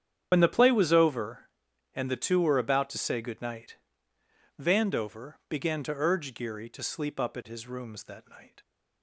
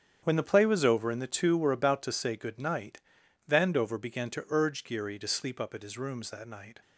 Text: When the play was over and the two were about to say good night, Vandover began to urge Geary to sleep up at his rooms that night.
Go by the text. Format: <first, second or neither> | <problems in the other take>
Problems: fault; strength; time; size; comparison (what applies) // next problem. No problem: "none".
second | loses the start of "When"; at 0.3 s; 55 ms // starts louder than the rest; strong; until 1.3 s; 8.5 dB; strong in the second